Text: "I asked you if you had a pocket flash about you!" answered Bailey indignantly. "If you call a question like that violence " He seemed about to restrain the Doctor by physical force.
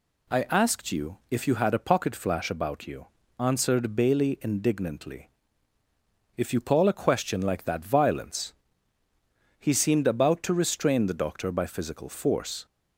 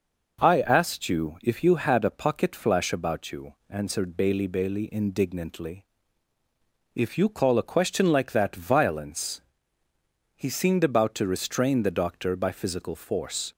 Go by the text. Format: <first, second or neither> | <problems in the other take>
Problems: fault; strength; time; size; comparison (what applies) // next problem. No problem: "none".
first | says "Bailey" twice; at 4.4 s